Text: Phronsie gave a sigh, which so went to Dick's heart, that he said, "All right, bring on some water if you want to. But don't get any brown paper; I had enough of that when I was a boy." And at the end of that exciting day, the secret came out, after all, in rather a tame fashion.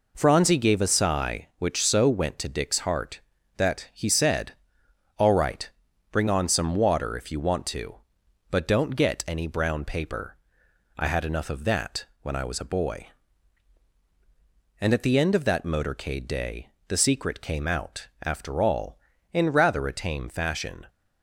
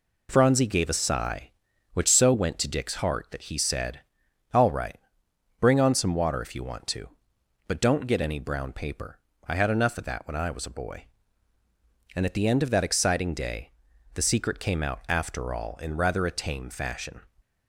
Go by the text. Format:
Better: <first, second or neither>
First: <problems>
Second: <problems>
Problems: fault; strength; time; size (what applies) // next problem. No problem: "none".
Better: second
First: pauses between "that" and "when"; slight; at 12.0 s; 0.18 s long // says "motorcade" for "exciting"; at 15.6 s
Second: none